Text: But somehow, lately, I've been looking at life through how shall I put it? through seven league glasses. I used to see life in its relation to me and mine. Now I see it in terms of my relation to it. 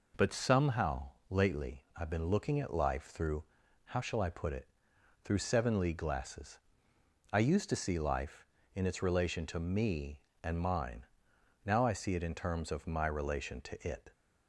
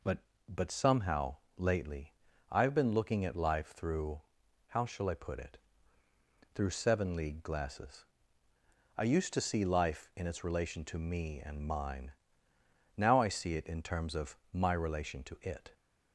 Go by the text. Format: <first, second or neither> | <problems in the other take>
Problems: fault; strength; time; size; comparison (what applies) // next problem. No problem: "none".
first | says "But" twice; at 0.4 s // pauses between "through" and "how"; noticeable; at 4.1 s; 0.48 s long; also in the first // pauses between "of" and "my"; slight; at 14.3 s; 0.16 s long